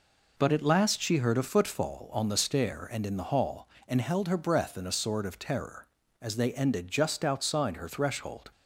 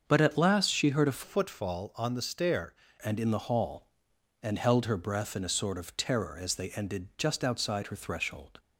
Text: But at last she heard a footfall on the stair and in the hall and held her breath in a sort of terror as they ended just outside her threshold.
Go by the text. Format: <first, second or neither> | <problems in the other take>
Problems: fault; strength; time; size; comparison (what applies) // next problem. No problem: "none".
first | starts louder than the rest; until 1.0 s; 6.5 dB // changes voice from "footfall" to "stair"; from 1.2 to 2.7 s; 1.5 s long